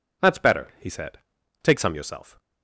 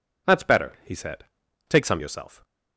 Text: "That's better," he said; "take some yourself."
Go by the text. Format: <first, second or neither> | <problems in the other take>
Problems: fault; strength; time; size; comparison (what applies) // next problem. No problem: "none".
neither | none